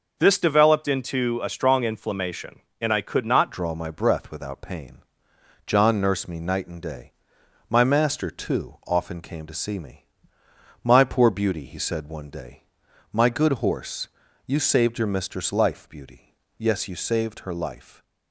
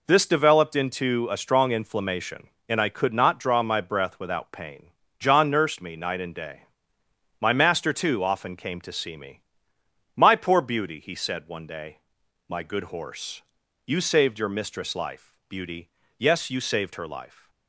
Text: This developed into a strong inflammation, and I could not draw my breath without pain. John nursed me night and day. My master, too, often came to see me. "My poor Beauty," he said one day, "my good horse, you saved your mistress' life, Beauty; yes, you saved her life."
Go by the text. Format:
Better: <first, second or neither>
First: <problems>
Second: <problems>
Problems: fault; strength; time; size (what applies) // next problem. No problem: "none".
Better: second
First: starts louder than the rest; until 1.2 s; 6 dB // changes voice at "draw"; from 3.5 s on; 14.5 s long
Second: none